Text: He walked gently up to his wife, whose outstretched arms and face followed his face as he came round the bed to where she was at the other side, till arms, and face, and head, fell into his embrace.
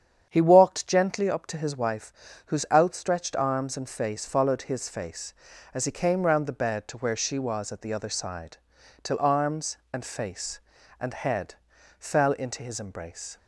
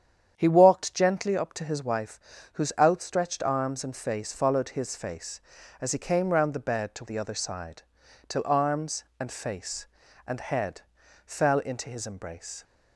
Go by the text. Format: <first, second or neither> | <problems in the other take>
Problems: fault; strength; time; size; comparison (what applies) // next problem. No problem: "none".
first | starts louder than the rest; strong; until 1.3 s; 8.5 dB; strong in the first // skips "where she was at"; at 7.0 s